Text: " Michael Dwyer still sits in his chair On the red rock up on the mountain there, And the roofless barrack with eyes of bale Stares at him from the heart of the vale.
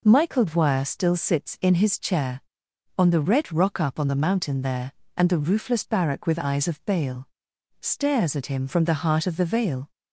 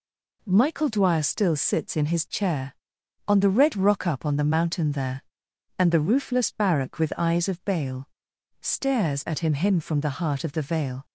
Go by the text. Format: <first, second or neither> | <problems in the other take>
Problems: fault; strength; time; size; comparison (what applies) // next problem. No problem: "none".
first | pauses between "bale" and "Stares"; noticeable; at 8.0 s; 0.52 s long; noticeable in the first // says "him" twice; at 9.5 s